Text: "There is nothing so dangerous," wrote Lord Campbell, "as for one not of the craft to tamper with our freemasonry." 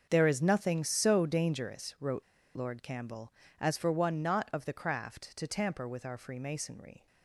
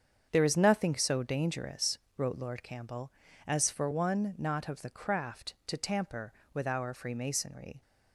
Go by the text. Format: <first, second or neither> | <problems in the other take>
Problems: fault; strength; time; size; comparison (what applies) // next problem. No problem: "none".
second | starts louder than the rest; until 1.1 s; 6.5 dB; strong in the second // pauses between "wrote" and "Lord"; slight; at 2.2 s; 0.30 s long